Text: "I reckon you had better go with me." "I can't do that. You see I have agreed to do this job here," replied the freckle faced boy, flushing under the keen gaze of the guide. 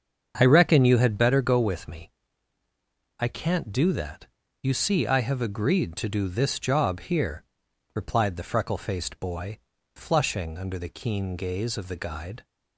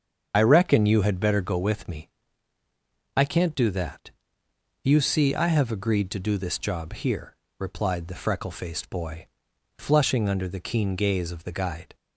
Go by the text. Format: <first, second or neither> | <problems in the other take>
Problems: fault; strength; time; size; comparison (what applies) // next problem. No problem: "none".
first | loses the start of "I"; at 0.3 s; 60 ms // starts louder than the rest; until 1.3 s; 7 dB; also in the first